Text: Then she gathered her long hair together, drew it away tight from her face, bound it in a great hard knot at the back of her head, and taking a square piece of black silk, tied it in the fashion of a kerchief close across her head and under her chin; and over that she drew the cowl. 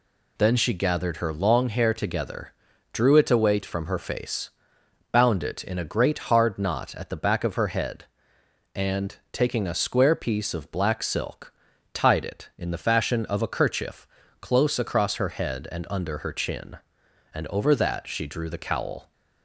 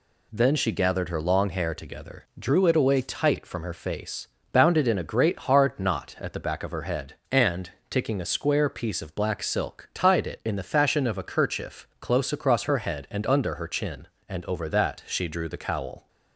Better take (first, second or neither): second